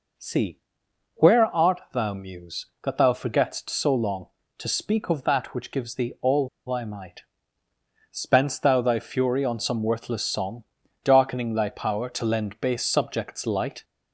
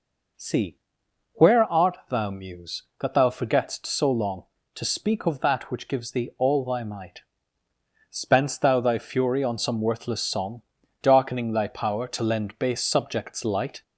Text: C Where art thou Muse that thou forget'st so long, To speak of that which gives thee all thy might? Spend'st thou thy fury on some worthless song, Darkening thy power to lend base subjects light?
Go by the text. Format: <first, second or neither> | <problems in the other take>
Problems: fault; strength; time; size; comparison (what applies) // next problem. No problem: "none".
second | pauses between "C" and "Where"; noticeable; at 0.5 s; 0.58 s long; noticeable in the second // pauses between "all" and "thy"; slight; at 6.4 s; 0.20 s long